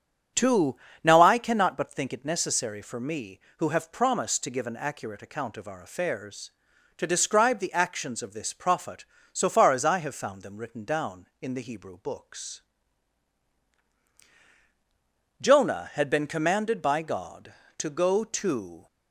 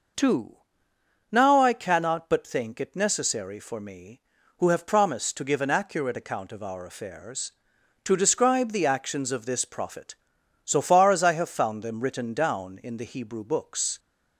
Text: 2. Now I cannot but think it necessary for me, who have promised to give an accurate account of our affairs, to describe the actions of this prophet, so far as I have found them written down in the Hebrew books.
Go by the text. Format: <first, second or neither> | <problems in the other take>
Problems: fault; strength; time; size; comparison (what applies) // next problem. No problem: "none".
second | starts louder than the rest; strong; until 1.6 s; 8.5 dB // goes on to say "Jonah had been commanded by God to go to"; strong; from 15.4 s on; 3.4 s long